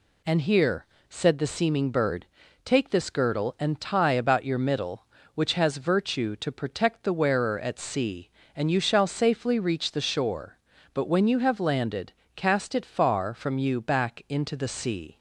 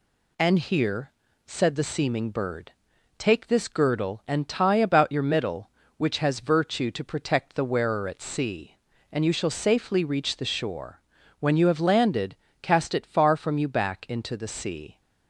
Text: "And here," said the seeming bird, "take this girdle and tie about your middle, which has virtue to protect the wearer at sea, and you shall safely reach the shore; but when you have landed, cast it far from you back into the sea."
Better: first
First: none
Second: skips "but"; at 11.2 s

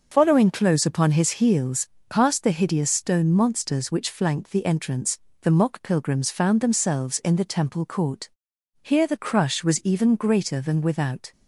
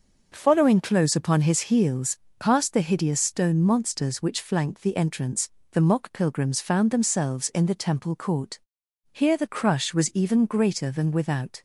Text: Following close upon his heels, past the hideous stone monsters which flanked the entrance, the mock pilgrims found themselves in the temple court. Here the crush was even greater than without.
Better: second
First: loses the start of "Following"; at 0.1 s; 85 ms // starts louder than the rest; noticeable; until 1.1 s; 6 dB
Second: starts louder than the rest; noticeable; until 1.3 s; 6 dB

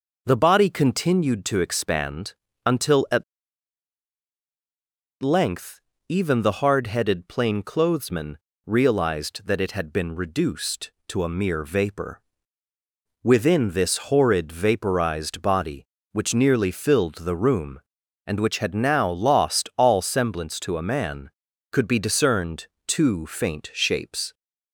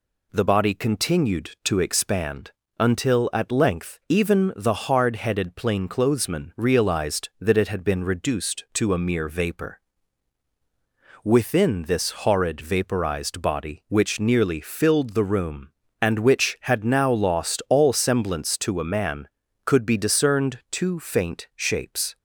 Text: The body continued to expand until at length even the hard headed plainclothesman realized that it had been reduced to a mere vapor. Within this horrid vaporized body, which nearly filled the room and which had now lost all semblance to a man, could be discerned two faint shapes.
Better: second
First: pauses between "expand" and "until"; slight; at 2.3 s; 0.32 s long // pauses between "at" and "length"; strong; at 3.2 s; 1.9 s long // pauses between "length" and "even"; slight; at 5.7 s; 0.30 s long // pauses between "plainclothesman" and "realized"; slight; at 8.3 s; 0.30 s long // pauses between "discerned" and "two"; slight; at 22.6 s; 0.18 s long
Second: pauses between "expand" and "until"; slight; at 2.5 s; 0.26 s long

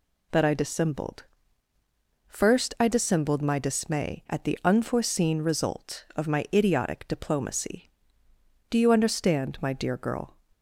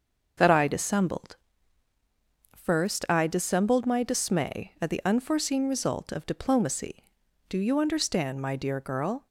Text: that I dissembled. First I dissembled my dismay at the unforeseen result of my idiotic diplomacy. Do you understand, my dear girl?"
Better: first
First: none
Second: starts louder than the rest; until 2.5 s; 6.5 dB // skips "my idiotic"; at 6.2 s

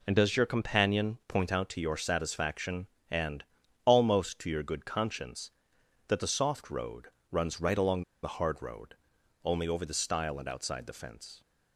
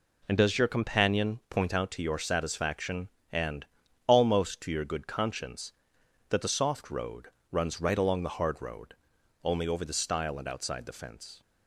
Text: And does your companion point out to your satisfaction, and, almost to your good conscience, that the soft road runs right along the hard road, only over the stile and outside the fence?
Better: second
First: pauses between "road" and "runs"; slight; at 7.0 s; 0.22 s long // pauses between "along" and "the"; slight; at 8.0 s; 0.20 s long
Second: pauses between "road" and "runs"; slight; at 7.2 s; 0.22 s long

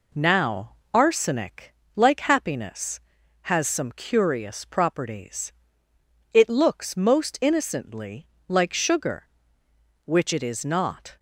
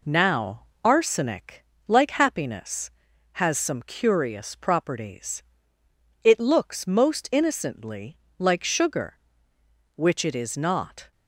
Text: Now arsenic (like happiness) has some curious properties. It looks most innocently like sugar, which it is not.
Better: neither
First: pauses between "Now" and "arsenic"; slight; at 0.7 s; 0.20 s long // pauses between "innocently" and "like"; slight; at 8.2 s; 0.22 s long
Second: pauses between "Now" and "arsenic"; slight; at 0.6 s; 0.20 s long // pauses between "innocently" and "like"; slight; at 8.1 s; 0.22 s long

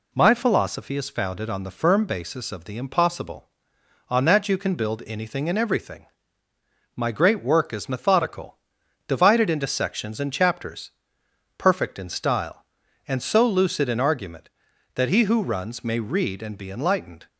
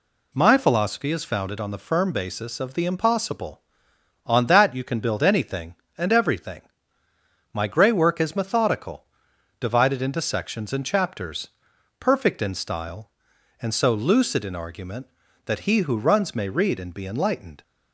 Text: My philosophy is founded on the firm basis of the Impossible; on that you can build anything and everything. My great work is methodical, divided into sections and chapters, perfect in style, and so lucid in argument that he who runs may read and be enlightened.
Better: first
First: none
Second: says "grey" for "great"; at 7.6 s

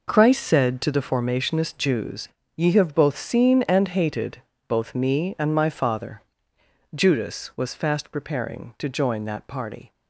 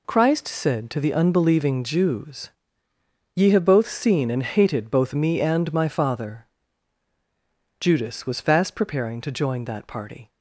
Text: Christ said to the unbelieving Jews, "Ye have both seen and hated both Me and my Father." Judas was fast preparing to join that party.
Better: second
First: says "formationist" for "unbelieving"; at 1.0 s // pauses between "hated" and "both"; slight; at 4.4 s; 0.26 s long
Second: none

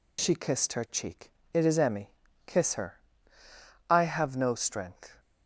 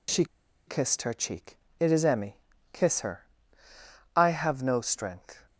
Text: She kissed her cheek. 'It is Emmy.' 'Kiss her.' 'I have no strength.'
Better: first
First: none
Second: pauses between "She" and "kissed"; at 0.2 s; 0.41 s long

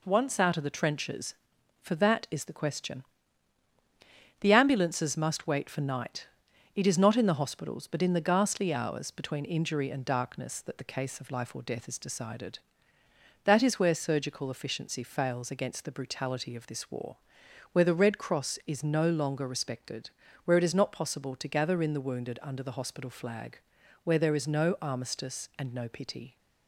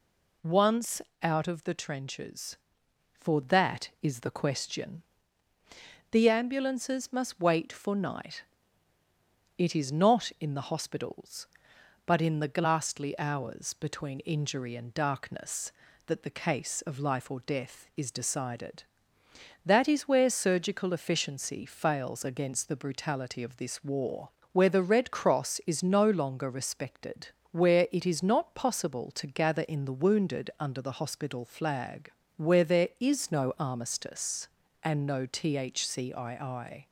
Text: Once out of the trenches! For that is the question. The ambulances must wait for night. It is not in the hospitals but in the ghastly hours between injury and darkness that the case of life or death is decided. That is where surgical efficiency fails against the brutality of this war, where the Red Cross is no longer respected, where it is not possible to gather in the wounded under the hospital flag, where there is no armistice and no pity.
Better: first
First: none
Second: pauses between "Once" and "out"; slight; at 1.0 s; 0.20 s long // says "thcii" for "pity"; at 35.2 s

